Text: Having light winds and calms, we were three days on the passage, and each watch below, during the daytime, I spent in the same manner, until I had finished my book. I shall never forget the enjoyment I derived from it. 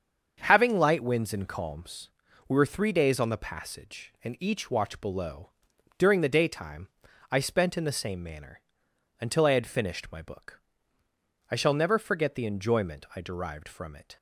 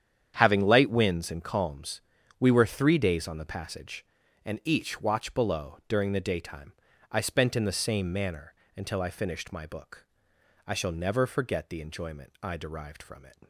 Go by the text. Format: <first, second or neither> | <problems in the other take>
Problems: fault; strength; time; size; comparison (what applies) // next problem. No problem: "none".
first | starts louder than the rest; strong; until 1.3 s; 9 dB; also in the first // skips "had"; at 9.1 s